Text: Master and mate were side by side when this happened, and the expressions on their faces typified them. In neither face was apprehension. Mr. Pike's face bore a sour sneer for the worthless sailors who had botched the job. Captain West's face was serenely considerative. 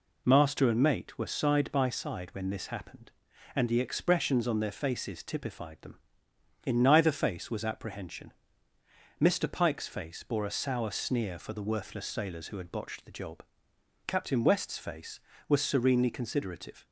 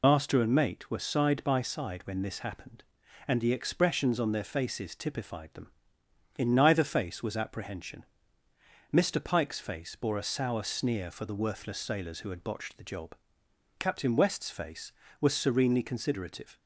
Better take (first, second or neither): first